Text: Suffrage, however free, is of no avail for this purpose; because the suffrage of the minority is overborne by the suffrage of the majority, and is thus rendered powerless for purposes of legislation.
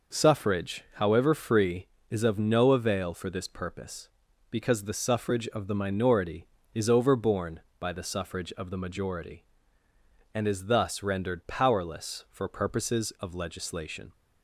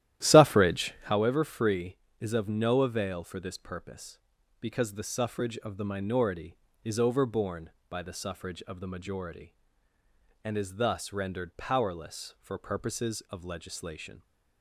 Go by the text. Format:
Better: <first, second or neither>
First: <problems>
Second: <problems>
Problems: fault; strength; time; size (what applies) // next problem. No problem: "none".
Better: first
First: none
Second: starts louder than the rest; strong; until 1.2 s; 13 dB